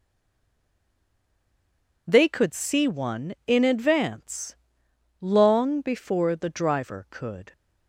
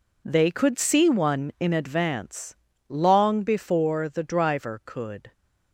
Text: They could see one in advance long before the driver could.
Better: second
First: stays silent before the first word; noticeable; until 2.0 s; 2.0 s long // pauses between "advance" and "long"; noticeable; at 4.5 s; 0.66 s long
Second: pauses between "advance" and "long"; slight; at 2.5 s; 0.32 s long

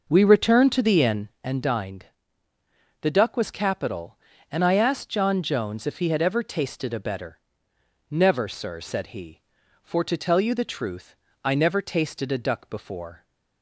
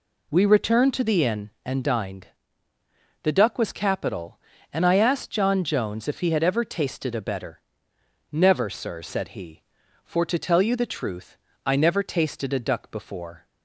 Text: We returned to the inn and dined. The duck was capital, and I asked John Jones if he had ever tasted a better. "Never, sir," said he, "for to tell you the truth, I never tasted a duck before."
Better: second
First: starts louder than the rest; noticeable; until 1.4 s; 5.5 dB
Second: none

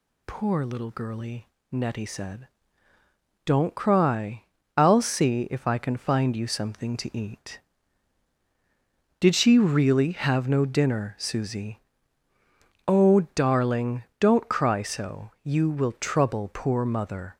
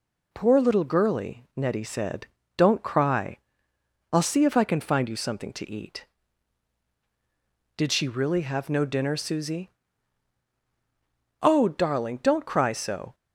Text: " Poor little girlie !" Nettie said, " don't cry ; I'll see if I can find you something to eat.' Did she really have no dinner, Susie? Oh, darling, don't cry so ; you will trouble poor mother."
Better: first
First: none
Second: stops before "you will trouble poor mother"; at 13.1 s

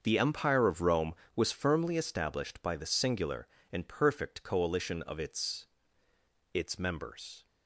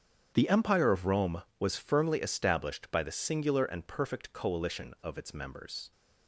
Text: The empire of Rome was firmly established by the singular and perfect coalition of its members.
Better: second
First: starts louder than the rest; until 1.0 s; 6.5 dB // says "its" twice; at 6.5 s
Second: starts louder than the rest; strong; until 1.3 s; 7.5 dB

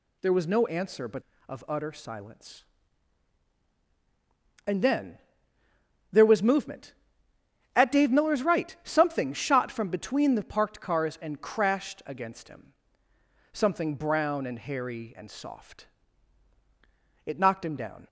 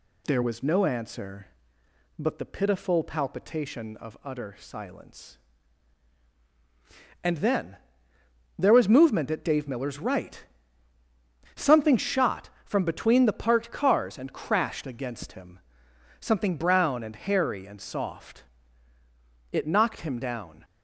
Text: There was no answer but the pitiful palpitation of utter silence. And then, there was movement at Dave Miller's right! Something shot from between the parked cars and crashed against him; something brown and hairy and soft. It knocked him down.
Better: second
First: skips "the pitiful palpitation"; at 1.3 s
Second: none

